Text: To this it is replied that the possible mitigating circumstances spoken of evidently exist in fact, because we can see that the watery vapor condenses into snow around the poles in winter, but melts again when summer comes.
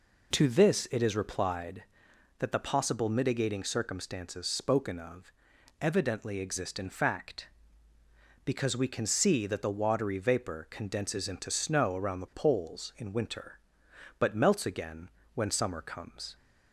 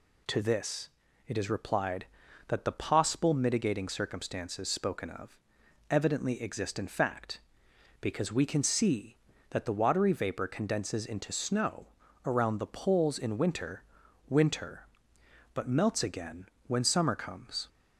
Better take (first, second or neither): first